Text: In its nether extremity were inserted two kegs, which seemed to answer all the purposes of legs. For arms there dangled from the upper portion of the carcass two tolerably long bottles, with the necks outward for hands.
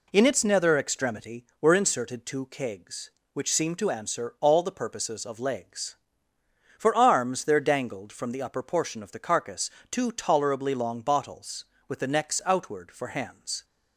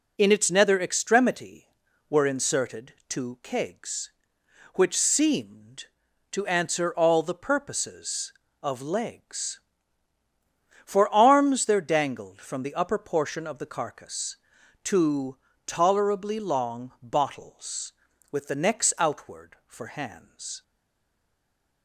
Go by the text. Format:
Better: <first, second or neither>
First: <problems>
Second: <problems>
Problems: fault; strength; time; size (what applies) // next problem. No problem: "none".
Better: first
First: pauses between "carcass" and "two"; slight; at 9.6 s; 0.22 s long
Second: pauses between "carcass" and "two"; noticeable; at 14.3 s; 0.46 s long // pauses between "two" and "tolerably"; slight; at 15.3 s; 0.28 s long // stays silent after the last word; noticeable; from 20.6 s on; 1.2 s long